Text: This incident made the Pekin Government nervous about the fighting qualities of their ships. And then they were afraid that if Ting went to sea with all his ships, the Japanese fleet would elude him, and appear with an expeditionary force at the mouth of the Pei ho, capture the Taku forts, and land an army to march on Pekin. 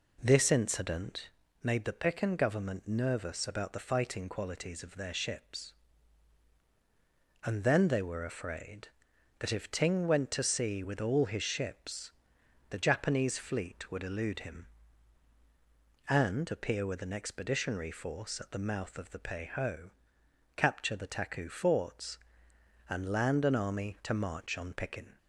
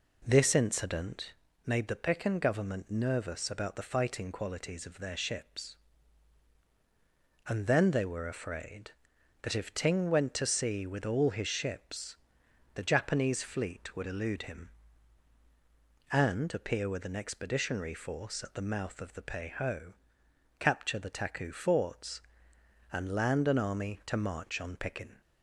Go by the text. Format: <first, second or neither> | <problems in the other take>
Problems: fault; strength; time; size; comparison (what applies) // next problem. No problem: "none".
neither | pauses between "incident" and "made"; slight; the same in both